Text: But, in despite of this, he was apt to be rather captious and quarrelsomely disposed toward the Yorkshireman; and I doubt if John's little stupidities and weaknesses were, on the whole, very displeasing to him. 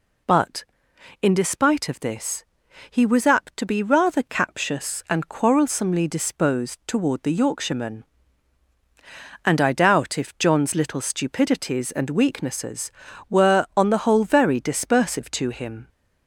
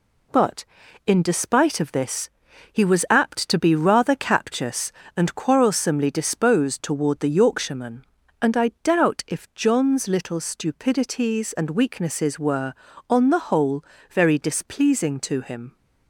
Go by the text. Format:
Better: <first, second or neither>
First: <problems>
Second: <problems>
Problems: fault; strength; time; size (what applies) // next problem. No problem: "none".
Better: second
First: says "dispersive" for "displeasing"; at 14.6 s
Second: none